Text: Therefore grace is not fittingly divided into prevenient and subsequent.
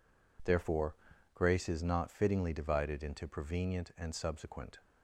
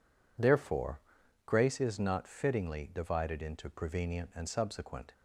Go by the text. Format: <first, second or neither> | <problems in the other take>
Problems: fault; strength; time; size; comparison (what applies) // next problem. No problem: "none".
neither | pauses between "Therefore" and "grace"; the same in both